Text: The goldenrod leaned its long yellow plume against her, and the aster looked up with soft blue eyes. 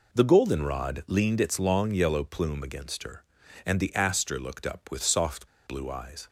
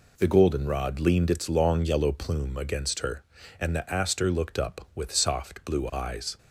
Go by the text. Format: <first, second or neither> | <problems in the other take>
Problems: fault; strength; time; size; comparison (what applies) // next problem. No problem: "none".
second | pauses between "soft" and "blue"; slight; at 5.4 s; 0.19 s long